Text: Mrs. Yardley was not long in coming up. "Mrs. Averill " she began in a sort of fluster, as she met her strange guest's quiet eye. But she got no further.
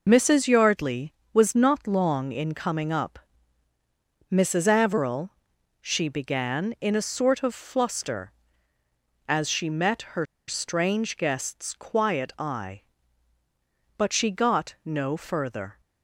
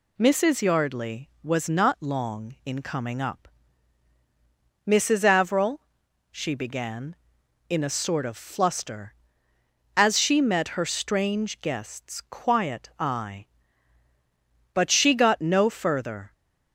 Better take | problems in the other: second | pauses between "her" and "strange"; slight; at 10.2 s; 0.24 s long

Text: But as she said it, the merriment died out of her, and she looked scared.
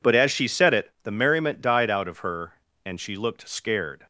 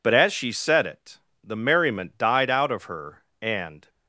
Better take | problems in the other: first | stops before "she looked scared"; at 3.8 s

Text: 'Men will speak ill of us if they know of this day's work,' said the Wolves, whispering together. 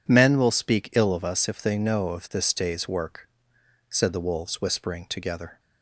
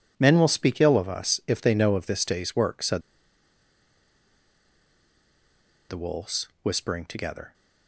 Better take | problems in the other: first | pauses between "said" and "the"; strong; at 3.0 s; 2.8 s long

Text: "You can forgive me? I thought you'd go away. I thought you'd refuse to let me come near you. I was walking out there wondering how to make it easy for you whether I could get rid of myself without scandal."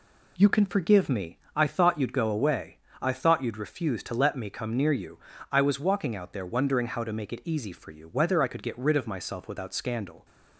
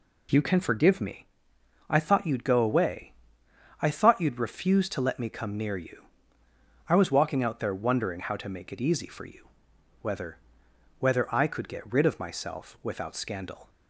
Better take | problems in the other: first | pauses between "you" and "whether"; noticeable; at 9.4 s; 0.56 s long // says "whether" twice; at 10.9 s

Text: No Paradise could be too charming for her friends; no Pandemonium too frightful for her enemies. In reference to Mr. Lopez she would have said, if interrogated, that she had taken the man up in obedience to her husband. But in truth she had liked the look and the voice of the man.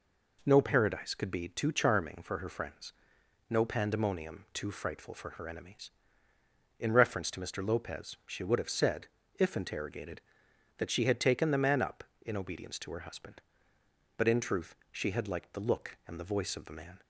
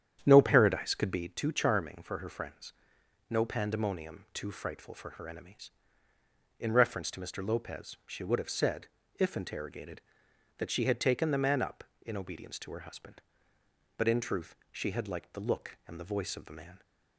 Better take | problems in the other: first | starts louder than the rest; strong; until 1.3 s; 9 dB // pauses between "truth" and "she"; slight; at 14.5 s; 0.18 s long; slight in the first

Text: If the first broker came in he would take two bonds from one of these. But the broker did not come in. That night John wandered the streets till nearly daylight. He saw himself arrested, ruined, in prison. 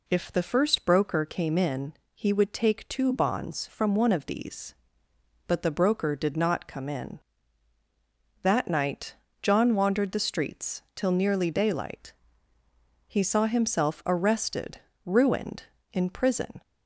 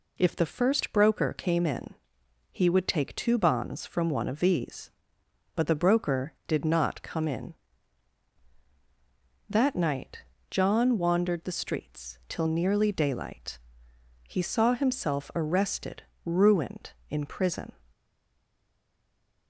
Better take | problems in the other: first | pauses between "in" and "he"; noticeable; at 1.9 s; 0.56 s long; slight in the first // pauses between "night" and "John"; slight; at 10.2 s; 0.28 s long; slight in the first // stays silent after the last word; noticeable; from 17.9 s on; 1.5 s long

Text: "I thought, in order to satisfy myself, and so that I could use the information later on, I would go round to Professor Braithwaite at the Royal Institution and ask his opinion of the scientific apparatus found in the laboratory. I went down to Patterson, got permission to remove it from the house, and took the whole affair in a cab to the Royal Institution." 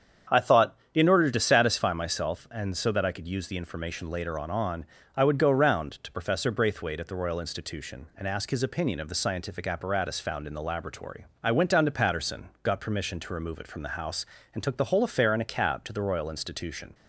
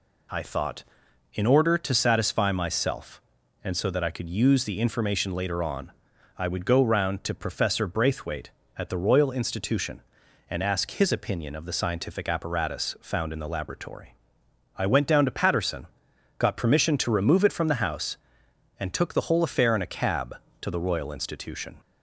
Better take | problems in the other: second | starts louder than the rest; strong; until 1.4 s; 7.5 dB // says "on" twice; at 4.5 s

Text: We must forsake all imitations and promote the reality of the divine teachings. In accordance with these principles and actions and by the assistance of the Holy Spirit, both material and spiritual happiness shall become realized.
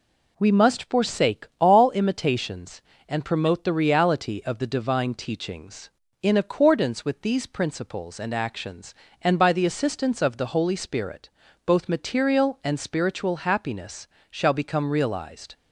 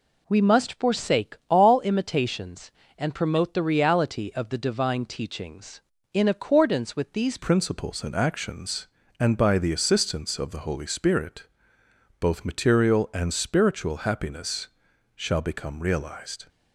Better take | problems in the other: first | changes voice at "principles"; from 7.3 s on; 9.1 s long // pauses between "happiness" and "shall"; noticeable; at 14.6 s; 0.48 s long; slight in the first

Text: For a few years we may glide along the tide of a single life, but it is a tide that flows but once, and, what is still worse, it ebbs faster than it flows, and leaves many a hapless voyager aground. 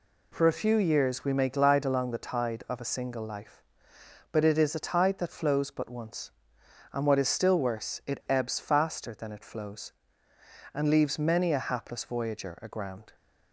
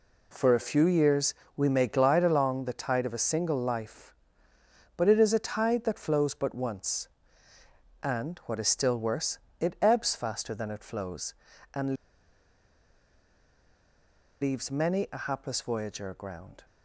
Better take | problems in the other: first | pauses between "years" and "we"; slight; at 1.3 s; 0.24 s long // pauses between "and" and "leaves"; strong; at 11.9 s; 2.4 s long

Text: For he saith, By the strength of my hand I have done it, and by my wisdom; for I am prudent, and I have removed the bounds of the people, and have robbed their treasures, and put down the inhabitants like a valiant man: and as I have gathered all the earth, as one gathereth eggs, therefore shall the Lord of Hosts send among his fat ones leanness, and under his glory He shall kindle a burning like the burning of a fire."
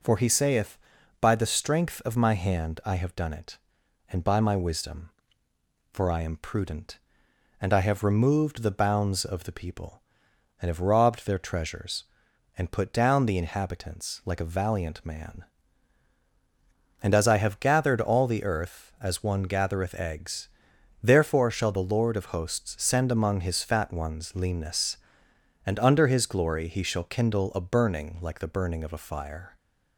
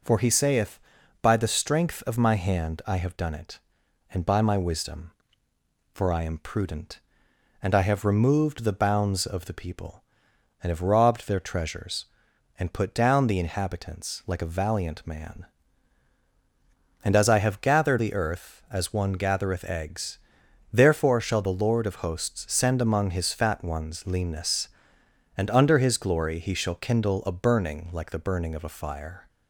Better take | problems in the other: first | skips "all"; at 17.9 s

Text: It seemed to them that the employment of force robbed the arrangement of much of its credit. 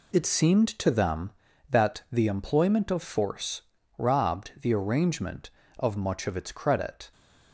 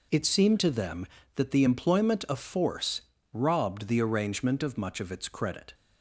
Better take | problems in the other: second | changes voice at "seemed"; from 0.2 s on; 6.9 s long // pauses between "force" and "robbed"; slight; at 3.6 s; 0.34 s long; slight in the second

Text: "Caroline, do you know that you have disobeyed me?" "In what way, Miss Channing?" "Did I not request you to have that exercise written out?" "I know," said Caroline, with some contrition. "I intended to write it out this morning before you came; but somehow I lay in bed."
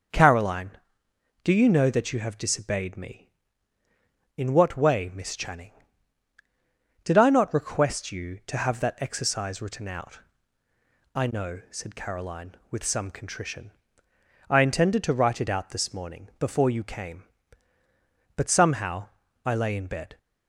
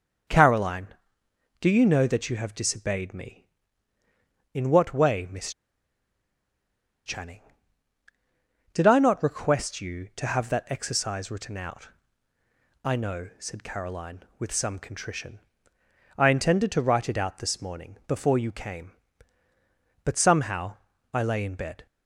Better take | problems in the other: first | starts louder than the rest; until 1.9 s; 6 dB; also in the first // pauses between "Miss" and "Channing"; strong; at 5.5 s; 1.5 s long // pauses between "somehow" and "I"; at 20.7 s; 0.38 s long; also in the first

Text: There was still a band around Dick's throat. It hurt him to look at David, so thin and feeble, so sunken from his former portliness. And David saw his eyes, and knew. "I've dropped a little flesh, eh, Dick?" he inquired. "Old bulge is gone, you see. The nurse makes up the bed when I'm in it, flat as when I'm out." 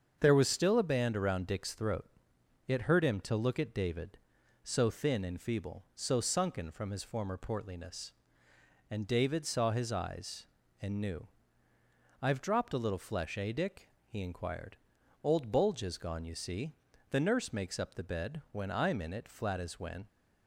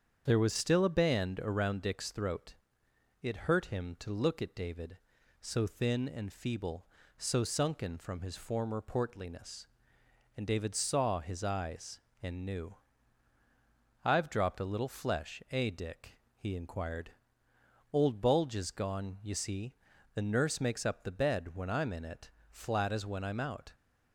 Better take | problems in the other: second | starts louder than the rest; until 1.2 s; 7 dB; strong in the second // stops before "I'm out"; at 20.0 s

